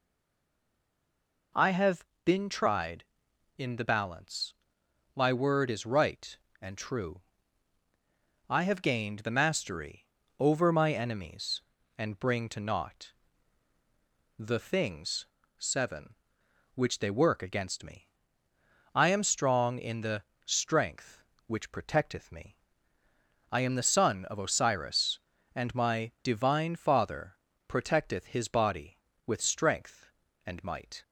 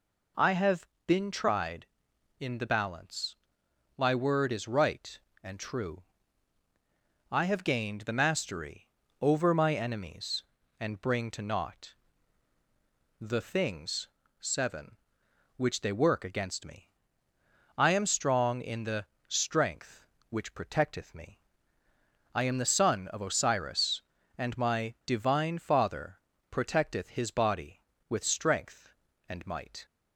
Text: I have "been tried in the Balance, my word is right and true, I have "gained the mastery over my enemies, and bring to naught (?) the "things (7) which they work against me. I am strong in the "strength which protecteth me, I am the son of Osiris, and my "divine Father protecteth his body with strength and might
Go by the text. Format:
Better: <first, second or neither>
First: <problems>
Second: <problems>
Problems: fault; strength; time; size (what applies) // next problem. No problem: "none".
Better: second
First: stays silent before the first word; noticeable; until 1.5 s; 1.5 s long // pauses between "have" and "been"; slight; at 2.0 s; 0.18 s long // pauses between "mastery" and "over"; slight; at 10.0 s; 0.34 s long // pauses between "the" and "strength"; slight; at 20.2 s; 0.22 s long // pauses between "Father" and "protecteth"; slight; at 27.3 s; 0.30 s long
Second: pauses between "have" and "been"; slight; at 0.8 s; 0.18 s long // pauses between "mastery" and "over"; slight; at 8.8 s; 0.34 s long // pauses between "the" and "strength"; slight; at 19.0 s; 0.22 s long // pauses between "Father" and "protecteth"; slight; at 26.1 s; 0.30 s long